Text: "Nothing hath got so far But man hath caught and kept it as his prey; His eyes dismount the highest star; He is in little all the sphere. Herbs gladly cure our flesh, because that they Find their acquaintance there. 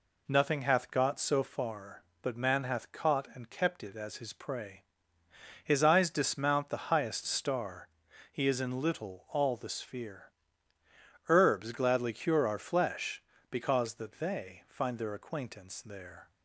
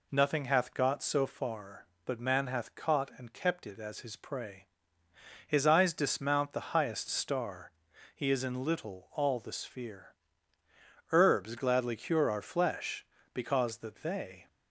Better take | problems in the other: first | stops before "Find their acquaintance there"; at 14.4 s

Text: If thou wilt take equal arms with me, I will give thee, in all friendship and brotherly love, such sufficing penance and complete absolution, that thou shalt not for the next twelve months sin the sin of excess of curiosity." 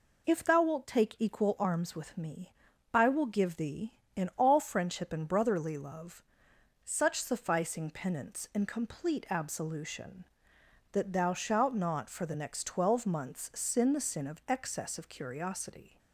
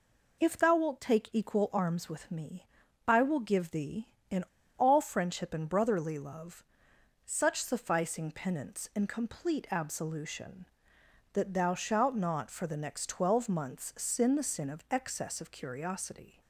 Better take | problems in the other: first | pauses between "in" and "all"; slight; at 4.4 s; 0.34 s long

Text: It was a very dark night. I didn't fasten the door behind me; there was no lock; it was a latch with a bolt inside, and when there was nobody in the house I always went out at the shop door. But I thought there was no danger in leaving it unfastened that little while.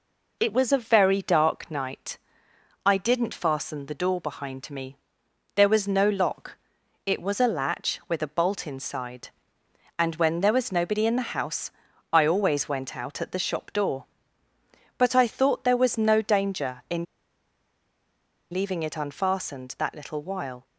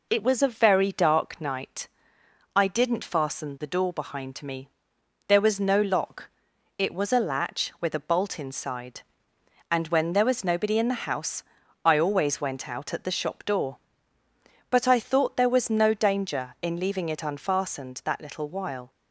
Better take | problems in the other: second | pauses between "house" and "I"; at 11.7 s; 0.40 s long; also in the second // pauses between "in" and "leaving"; strong; at 17.0 s; 1.4 s long

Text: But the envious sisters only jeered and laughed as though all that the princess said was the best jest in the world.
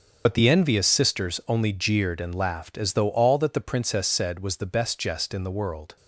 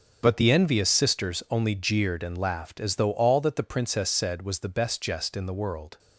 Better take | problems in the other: second | loses the start of "But"; at 0.2 s; 45 ms // starts louder than the rest; until 1.2 s; 6.5 dB; also in the second

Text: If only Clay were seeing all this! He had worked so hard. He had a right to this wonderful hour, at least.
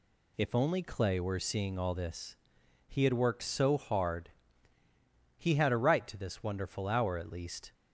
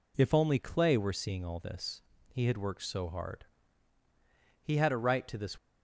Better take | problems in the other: first | stops before "wonderful hour at least"; at 5.5 s

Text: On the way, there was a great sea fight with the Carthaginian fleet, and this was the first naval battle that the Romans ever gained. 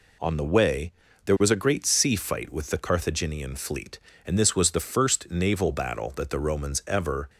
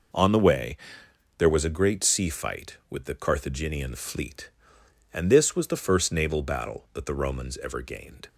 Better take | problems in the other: second | stops before "gained"; at 7.2 s

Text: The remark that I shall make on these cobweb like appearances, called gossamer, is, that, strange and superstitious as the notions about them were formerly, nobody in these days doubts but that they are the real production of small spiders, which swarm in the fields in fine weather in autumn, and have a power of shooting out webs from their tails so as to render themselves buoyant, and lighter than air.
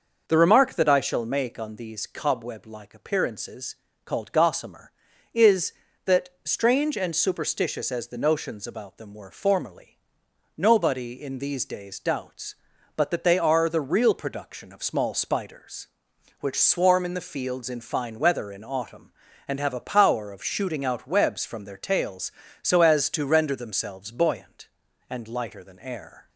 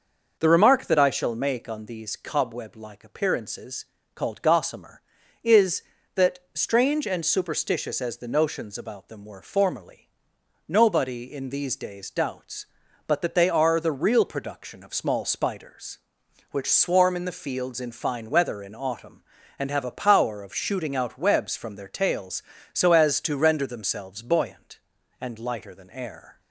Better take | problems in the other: neither | starts louder than the rest; noticeable; the same in both

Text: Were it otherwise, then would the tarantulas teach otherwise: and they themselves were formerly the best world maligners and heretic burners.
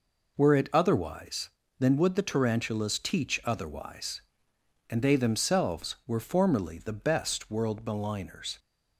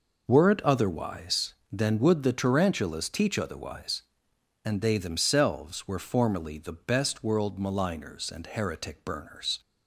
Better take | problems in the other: second | stops before "and heretic burners"; at 8.5 s

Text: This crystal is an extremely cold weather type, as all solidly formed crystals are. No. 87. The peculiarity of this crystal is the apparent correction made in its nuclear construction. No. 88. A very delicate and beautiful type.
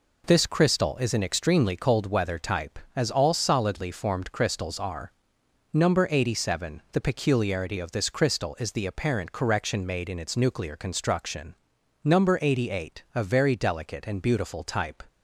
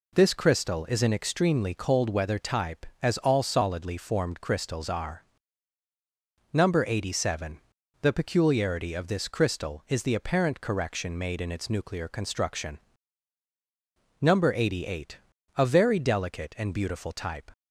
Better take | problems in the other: neither | none

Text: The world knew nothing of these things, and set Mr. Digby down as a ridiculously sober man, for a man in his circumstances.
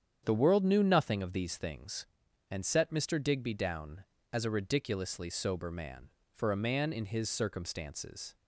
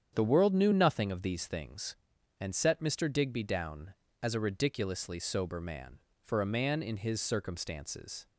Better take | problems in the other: neither | starts louder than the rest; strong; the same in both

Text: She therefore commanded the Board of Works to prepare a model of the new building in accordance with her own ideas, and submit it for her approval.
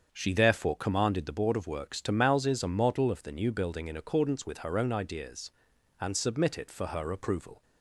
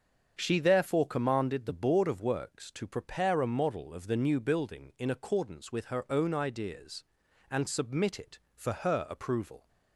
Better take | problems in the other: second | starts louder than the rest; strong; until 1.1 s; 7.5 dB; also in the second // says "mouses" for "prepare"; at 2.1 s

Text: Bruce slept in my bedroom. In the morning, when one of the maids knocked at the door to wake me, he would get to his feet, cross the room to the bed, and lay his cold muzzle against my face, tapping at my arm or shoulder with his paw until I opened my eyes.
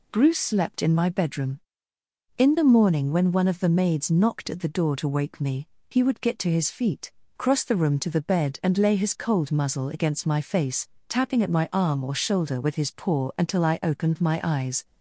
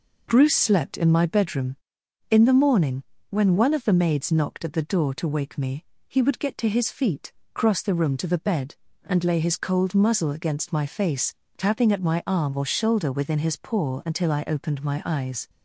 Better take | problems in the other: first | says "within" for "with"; at 13.1 s

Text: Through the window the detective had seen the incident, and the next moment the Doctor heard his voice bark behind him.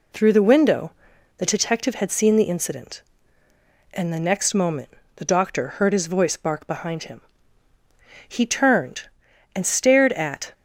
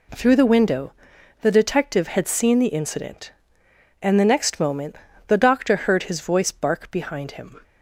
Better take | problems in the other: second | pauses between "window" and "the"; noticeable; at 0.9 s; 0.46 s long; noticeable in the second // pauses between "moment" and "the"; slight; at 4.8 s; 0.26 s long; slight in the second // goes on to say "He turned and stared at"; strong; from 8.2 s on; 2.2 s long

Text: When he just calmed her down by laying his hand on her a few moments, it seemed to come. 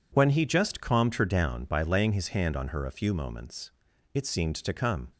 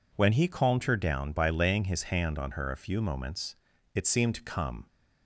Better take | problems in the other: first | skips "just"; at 0.4 s

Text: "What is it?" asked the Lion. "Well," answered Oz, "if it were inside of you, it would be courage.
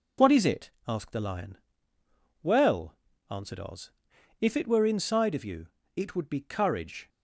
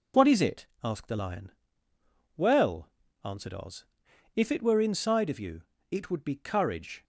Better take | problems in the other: neither | none

